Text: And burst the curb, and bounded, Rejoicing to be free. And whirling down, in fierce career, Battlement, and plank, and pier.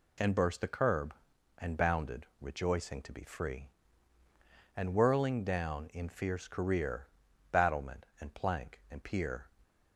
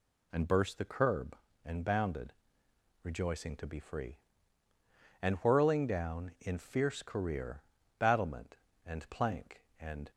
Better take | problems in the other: first | stops before "pier"; at 10.1 s

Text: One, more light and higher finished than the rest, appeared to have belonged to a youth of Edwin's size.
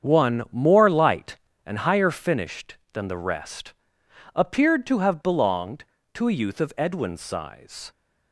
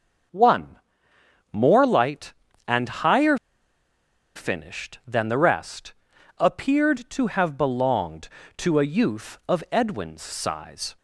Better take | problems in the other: first | starts louder than the rest; until 2.0 s; 7 dB; strong in the first // pauses between "higher" and "finished"; at 3.3 s; 1.0 s long

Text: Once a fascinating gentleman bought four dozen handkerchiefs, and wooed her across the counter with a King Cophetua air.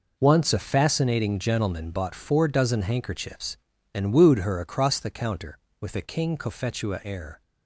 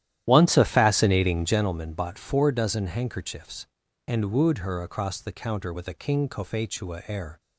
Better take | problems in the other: first | starts louder than the rest; strong; until 1.7 s; 12 dB

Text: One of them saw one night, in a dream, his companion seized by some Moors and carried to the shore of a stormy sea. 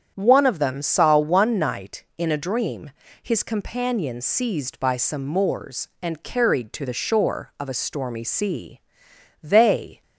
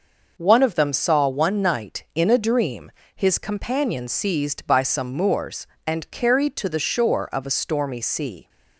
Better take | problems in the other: second | starts louder than the rest; strong; until 1.1 s; 8.5 dB // goes on to say "They"; from 9.4 s on; 0.60 s long

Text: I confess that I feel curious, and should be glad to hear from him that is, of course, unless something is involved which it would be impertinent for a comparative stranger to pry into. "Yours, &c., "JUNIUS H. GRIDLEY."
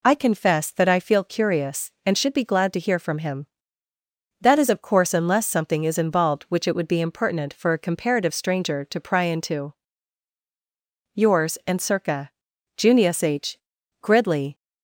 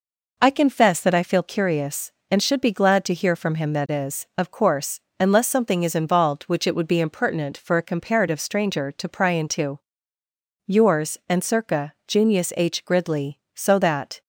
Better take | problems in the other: first | goes on to say "So that"; noticeable; from 13.5 s on; 0.68 s long

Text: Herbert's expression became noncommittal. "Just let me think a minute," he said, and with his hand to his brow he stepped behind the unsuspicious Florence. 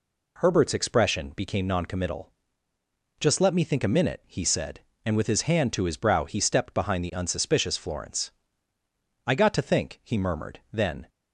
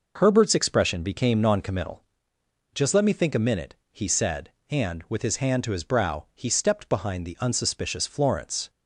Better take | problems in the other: second | goes on to say "I got to think he murmured then"; strong; from 9.2 s on; 1.8 s long

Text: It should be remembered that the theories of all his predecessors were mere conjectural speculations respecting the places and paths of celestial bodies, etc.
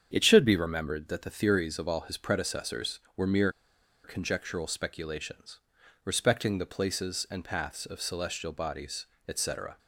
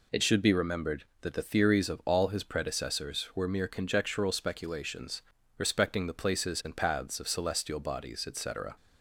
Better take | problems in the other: second | starts louder than the rest; strong; until 1.1 s; 7.5 dB // pauses between "mere" and "conjectural"; noticeable; at 3.5 s; 0.54 s long // pauses between "speculations" and "respecting"; noticeable; at 5.5 s; 0.48 s long; also in the second

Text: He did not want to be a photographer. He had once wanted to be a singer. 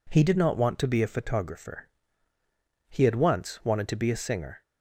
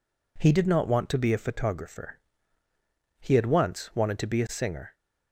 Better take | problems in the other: neither | none

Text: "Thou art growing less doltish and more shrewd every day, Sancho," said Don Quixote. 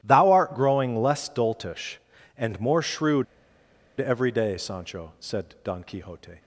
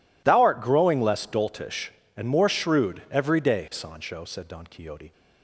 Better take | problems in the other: second | starts louder than the rest; strong; until 1.0 s; 13 dB // pauses between "shrewd" and "every"; noticeable; at 3.2 s; 0.74 s long

